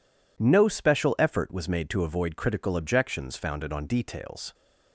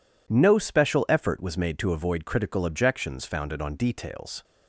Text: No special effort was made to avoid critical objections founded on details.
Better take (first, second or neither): neither